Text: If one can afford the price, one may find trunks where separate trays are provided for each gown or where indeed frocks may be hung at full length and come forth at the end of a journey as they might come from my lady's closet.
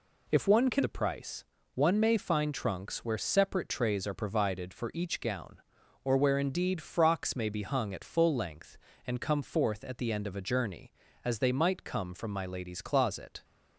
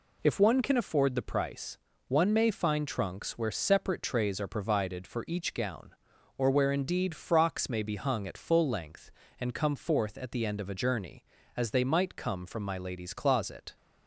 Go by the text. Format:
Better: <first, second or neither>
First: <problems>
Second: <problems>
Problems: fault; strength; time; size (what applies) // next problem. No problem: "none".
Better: second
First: skips "afford"; at 0.8 s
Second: none